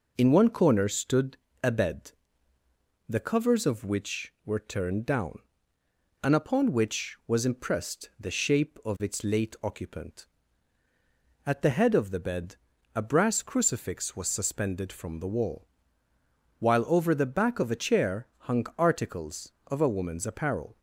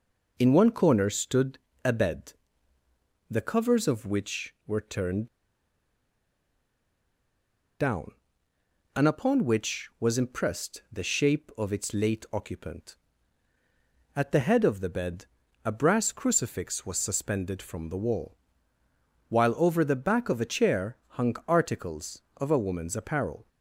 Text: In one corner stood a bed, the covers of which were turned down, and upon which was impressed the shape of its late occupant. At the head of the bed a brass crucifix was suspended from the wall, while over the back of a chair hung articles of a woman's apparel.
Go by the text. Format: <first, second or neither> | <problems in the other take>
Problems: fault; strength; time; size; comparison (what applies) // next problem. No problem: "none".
first | pauses between "stood" and "a"; slight; at 1.5 s; 0.26 s long; slight in the first // pauses between "turned" and "down"; strong; at 5.2 s; 2.5 s long // pauses between "bed" and "a"; at 15.2 s; 0.40 s long; also in the first